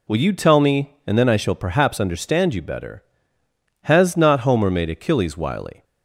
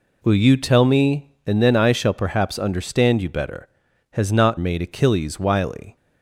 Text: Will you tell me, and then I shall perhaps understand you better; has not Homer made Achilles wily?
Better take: first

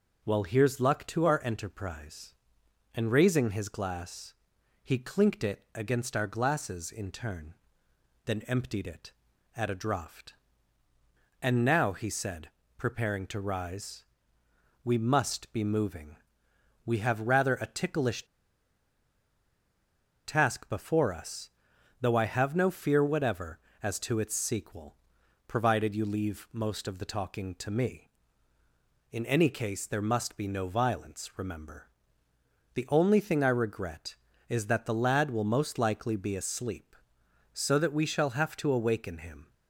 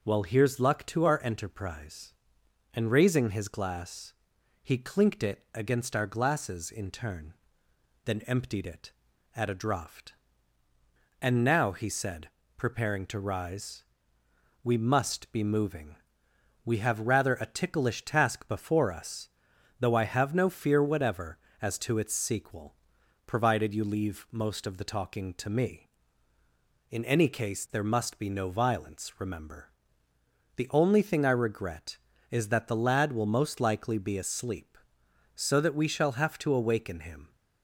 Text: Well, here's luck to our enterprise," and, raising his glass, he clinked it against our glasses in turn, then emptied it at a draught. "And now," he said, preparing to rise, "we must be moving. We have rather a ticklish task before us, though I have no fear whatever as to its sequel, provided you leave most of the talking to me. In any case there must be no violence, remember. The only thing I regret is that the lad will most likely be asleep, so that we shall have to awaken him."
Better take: second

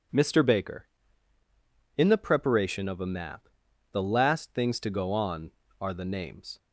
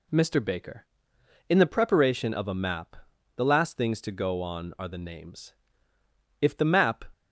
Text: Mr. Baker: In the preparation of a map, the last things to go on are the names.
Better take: first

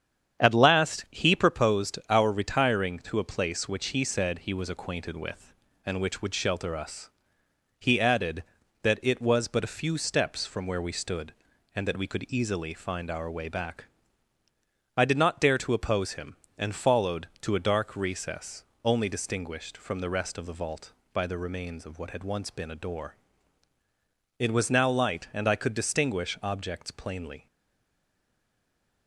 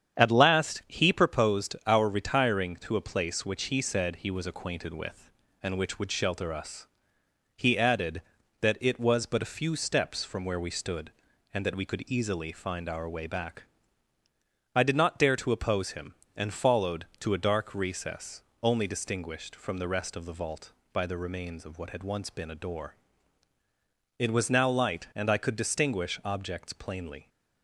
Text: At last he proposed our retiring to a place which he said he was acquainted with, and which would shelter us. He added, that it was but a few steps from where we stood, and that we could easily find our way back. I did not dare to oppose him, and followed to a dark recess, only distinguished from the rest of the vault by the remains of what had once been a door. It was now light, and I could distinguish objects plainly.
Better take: second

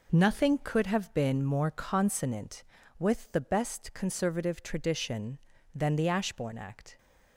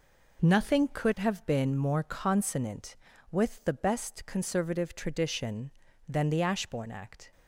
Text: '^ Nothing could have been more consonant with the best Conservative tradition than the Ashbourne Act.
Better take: neither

